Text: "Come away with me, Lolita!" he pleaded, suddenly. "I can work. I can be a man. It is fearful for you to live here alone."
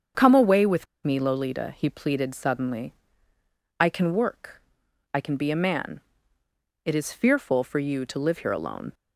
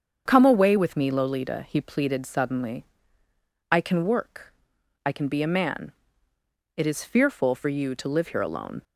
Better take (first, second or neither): second